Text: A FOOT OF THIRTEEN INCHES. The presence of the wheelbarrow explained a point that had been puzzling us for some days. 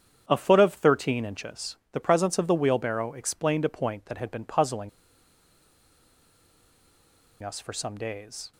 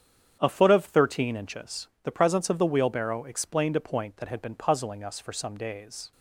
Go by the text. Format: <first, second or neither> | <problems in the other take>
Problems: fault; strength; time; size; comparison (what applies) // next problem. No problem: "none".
second | starts louder than the rest; strong; until 1.2 s; 8.5 dB; strong in the second // pauses between "puzzling" and "us"; strong; at 4.8 s; 2.5 s long